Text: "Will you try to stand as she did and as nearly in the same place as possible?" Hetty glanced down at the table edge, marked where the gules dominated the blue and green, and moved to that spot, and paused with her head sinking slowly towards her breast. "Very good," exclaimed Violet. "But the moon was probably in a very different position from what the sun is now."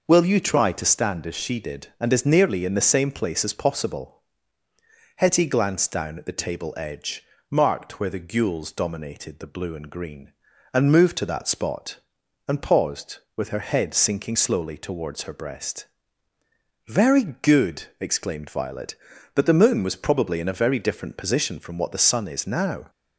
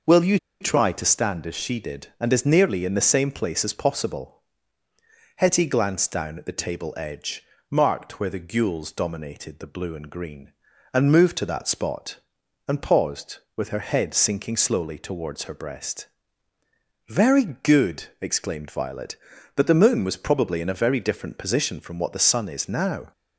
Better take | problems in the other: first | pauses between "you" and "try"; slight; at 0.3 s; 0.24 s long

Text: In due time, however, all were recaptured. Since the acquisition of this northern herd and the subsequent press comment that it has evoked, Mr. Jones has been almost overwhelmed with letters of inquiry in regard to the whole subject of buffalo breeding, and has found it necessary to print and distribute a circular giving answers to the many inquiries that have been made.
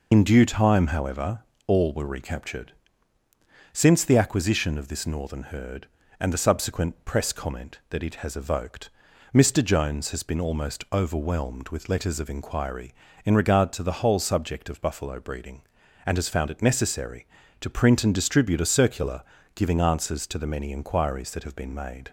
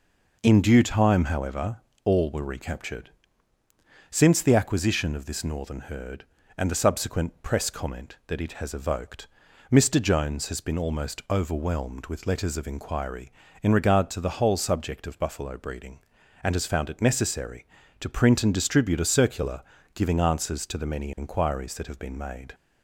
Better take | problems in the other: second | loses the start of "In"; at 0.1 s; 85 ms // pauses between "circular" and "giving"; slight; at 19.2 s; 0.32 s long; slight in the second

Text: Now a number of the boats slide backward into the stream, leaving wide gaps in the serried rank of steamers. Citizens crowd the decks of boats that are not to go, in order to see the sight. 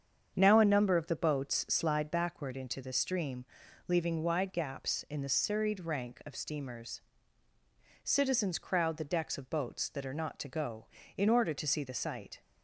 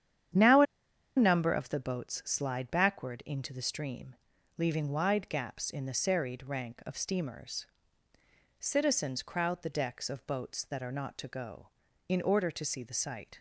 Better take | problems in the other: first | starts louder than the rest; strong; until 1.9 s; 9.5 dB; strong in the first // pauses between "a" and "number"; noticeable; at 0.6 s; 0.52 s long

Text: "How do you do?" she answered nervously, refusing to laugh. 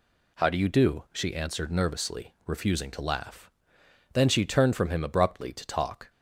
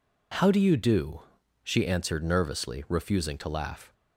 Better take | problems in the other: second | goes on to say "Then she turned from him abruptly to talk"; strong; from 4.1 s on; 1.9 s long

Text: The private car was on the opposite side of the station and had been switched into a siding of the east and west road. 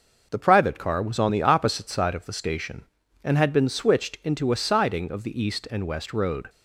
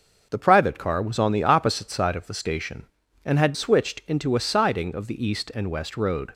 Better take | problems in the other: first | skips "been"; at 3.5 s

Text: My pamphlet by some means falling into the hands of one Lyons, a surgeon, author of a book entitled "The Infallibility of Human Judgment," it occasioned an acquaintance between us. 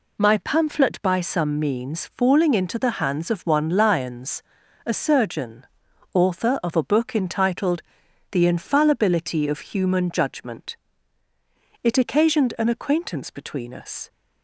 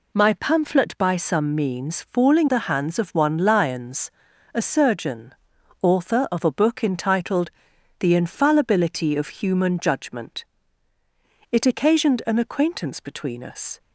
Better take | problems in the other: first | skips "into"; at 2.4 s // pauses between "entitled" and "The"; noticeable; at 7.4 s; 0.50 s long; noticeable in the first

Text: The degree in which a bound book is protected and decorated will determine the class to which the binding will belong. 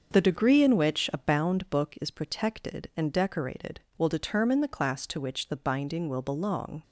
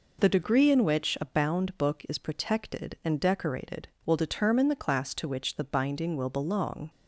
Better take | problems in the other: second | starts louder than the rest; until 1.9 s; 6.5 dB

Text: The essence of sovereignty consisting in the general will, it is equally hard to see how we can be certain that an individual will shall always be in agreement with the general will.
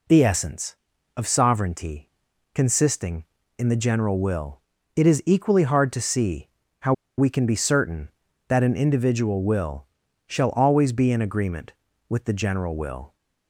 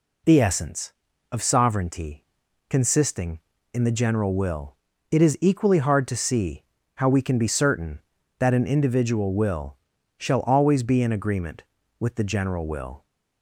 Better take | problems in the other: second | pauses between "sovereignty" and "consisting"; at 2.1 s; 0.44 s long; also in the second // pauses between "see" and "how"; slight; at 6.4 s; 0.32 s long; slight in the second // pauses between "how" and "we"; slight; at 6.9 s; 0.25 s long // pauses between "will" and "shall"; at 9.8 s; 0.42 s long; also in the second

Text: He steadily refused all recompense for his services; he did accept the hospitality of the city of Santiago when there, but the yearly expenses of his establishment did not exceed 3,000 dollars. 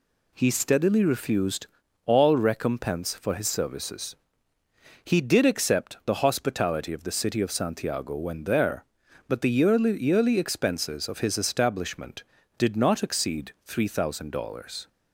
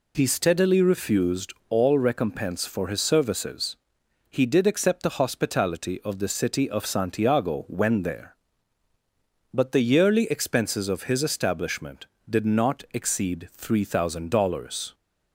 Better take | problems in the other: second | pauses between "refused" and "all"; at 1.6 s; 0.38 s long; slight in the second // says "yearly" twice; at 10.0 s

